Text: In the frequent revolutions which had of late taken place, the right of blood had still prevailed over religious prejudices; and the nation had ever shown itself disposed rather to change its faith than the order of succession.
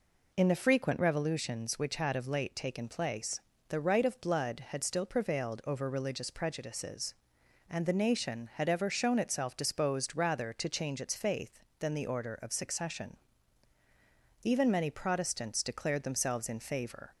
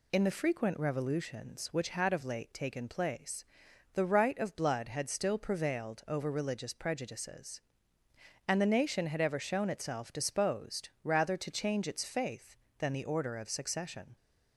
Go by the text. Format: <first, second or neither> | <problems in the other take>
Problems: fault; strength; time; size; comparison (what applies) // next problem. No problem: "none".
second | goes on to say "Even many Protestants declared themselves in favor"; strong; from 14.4 s on; 2.7 s long